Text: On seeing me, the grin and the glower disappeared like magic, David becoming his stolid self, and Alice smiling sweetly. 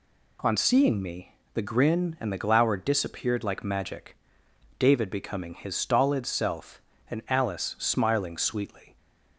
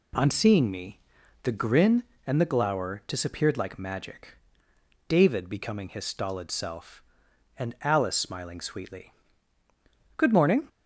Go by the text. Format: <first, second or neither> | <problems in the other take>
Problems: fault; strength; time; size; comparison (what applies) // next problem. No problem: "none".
first | goes on to say "Good morning"; from 10.1 s on; 0.52 s long